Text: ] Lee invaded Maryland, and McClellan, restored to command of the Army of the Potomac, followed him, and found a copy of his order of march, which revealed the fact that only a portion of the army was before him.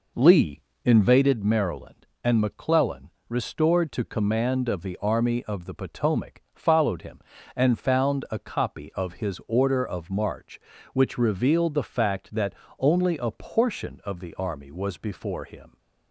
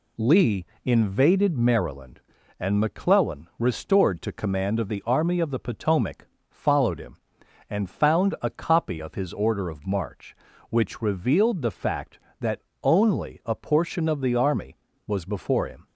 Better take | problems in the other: second | starts louder than the rest; noticeable; until 1.4 s; 4.5 dB // pauses between "Lee" and "invaded"; slight; at 0.6 s; 0.22 s long; slight in the second // pauses between "that" and "only"; slight; at 12.5 s; 0.24 s long; slight in the second

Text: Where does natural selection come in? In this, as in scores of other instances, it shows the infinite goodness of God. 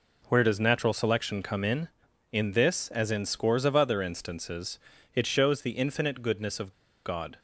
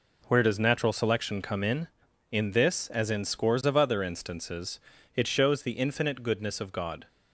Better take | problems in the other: second | pauses between "of" and "God"; slight; at 6.7 s; 0.34 s long

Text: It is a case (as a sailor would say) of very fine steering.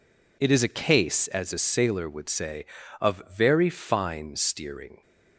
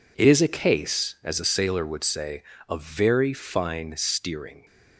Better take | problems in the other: neither | none

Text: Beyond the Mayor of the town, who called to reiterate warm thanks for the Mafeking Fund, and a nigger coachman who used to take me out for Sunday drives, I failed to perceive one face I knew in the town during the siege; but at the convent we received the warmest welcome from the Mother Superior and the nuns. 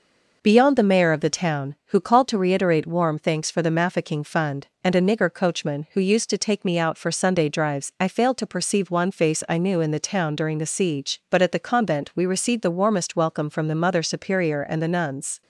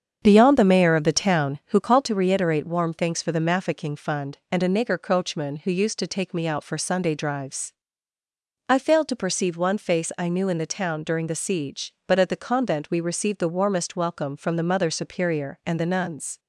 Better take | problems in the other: first | starts louder than the rest; strong; until 2.1 s; 7.5 dB

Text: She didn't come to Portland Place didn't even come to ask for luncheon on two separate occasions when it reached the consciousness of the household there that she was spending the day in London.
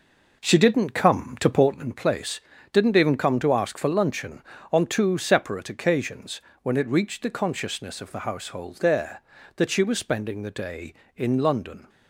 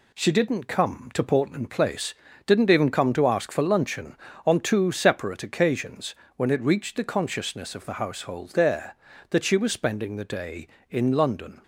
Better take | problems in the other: second | starts louder than the rest; noticeable; until 1.9 s; 5 dB // pauses between "Place" and "didn't"; slight; at 2.4 s; 0.30 s long; slight in the second // pauses between "occasions" and "when"; slight; at 6.3 s; 0.22 s long; slight in the second

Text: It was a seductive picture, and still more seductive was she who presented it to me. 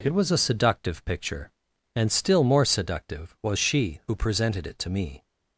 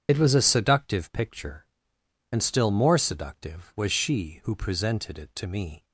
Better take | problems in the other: first | loses the start of "It"; at 0.0 s; 40 ms // starts louder than the rest; strong; until 1.1 s; 8 dB

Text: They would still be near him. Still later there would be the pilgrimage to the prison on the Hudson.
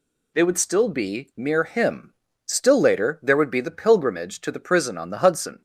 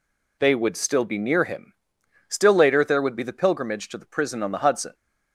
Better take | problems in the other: second | says "mere" for "near"; at 1.3 s

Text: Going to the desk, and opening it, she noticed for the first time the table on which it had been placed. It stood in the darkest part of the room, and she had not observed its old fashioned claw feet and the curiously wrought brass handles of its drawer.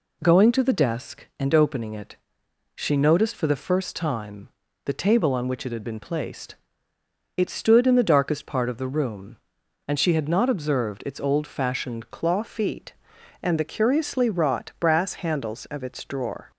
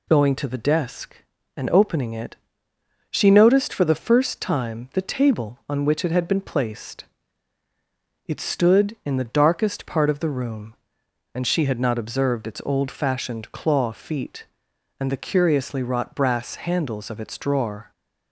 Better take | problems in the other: second | pauses between "time" and "the"; slight; at 4.5 s; 0.34 s long // changes voice at "claw"; from 12.1 s on; 4.4 s long

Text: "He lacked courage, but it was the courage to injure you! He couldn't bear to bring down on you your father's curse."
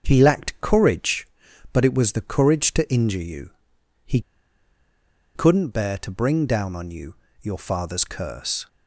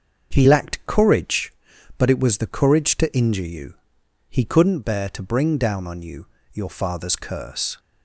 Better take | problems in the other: second | starts louder than the rest; until 1.0 s; 6.5 dB; also in the second // pauses between "He" and "couldn't"; at 4.2 s; 1.1 s long // pauses between "you" and "your"; slight; at 7.1 s; 0.26 s long; slight in the second

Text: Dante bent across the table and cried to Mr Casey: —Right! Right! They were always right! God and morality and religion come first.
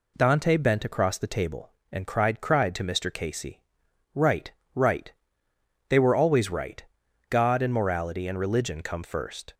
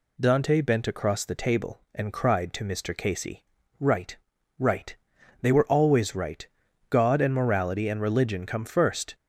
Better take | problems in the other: second | says "cried" twice; at 2.3 s

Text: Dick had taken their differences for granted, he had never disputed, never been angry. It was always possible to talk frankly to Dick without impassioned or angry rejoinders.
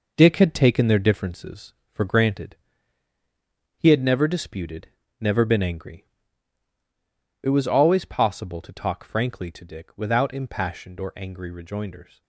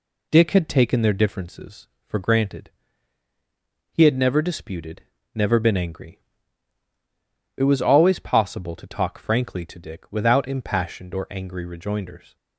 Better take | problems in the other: second | gets quieter; throughout; 6.5 dB

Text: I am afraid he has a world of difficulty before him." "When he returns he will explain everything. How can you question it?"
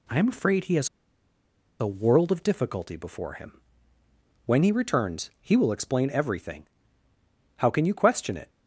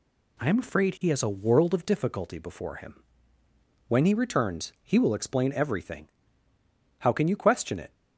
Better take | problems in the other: second | pauses between "has" and "a"; noticeable; at 0.8 s; 0.92 s long

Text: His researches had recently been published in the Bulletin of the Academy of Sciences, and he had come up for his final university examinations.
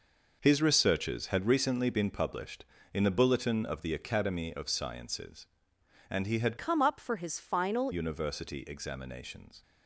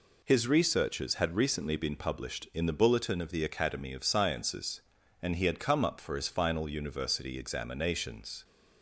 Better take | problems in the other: second | changes voice from "come" to "final"; from 6.5 to 7.9 s; 1.4 s long

